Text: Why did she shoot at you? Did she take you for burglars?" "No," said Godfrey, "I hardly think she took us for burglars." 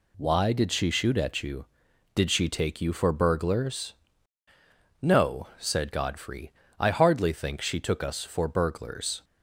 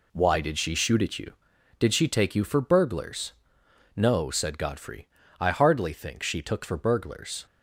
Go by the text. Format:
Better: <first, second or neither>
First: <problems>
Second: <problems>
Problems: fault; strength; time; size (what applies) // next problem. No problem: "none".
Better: first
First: none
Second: skips "us"; at 6.6 s